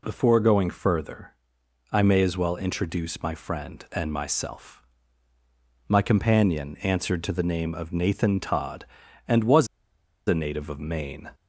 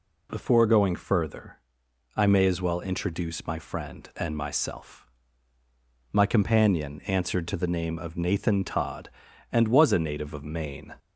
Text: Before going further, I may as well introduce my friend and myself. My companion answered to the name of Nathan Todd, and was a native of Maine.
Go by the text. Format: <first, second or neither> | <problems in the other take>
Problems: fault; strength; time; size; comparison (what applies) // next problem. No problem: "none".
second | pauses between "was" and "a"; noticeable; at 9.6 s; 0.60 s long